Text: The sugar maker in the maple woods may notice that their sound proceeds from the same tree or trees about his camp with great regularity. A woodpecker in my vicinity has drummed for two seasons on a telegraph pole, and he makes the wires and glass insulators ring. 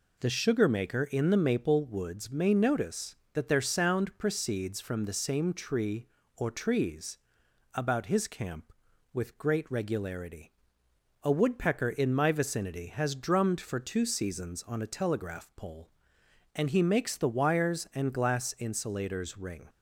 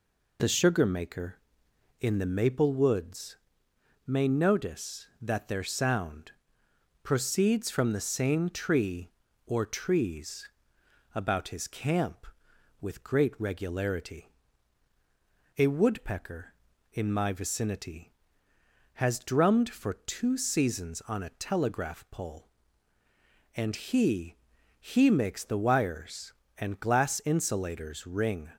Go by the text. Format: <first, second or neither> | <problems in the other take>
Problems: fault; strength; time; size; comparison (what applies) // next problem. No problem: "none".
first | pauses between "woods" and "may"; noticeable; at 3.3 s; 0.70 s long // pauses between "sound" and "proceeds"; noticeable; at 6.3 s; 0.72 s long // pauses between "trees" and "about"; noticeable; at 10.4 s; 0.64 s long; noticeable in the first // says "he" twice; at 24.7 s